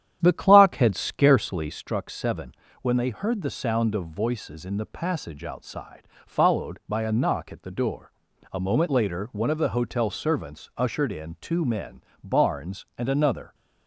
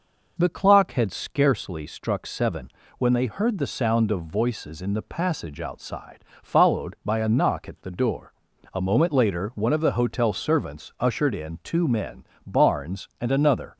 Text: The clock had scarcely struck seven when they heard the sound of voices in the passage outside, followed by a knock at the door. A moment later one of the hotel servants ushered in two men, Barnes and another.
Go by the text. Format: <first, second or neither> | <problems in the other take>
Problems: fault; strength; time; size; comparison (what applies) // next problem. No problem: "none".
second | starts louder than the rest; strong; until 1.9 s; 10 dB // pauses between "seven" and "when"; slight; at 2.5 s; 0.30 s long; slight in the second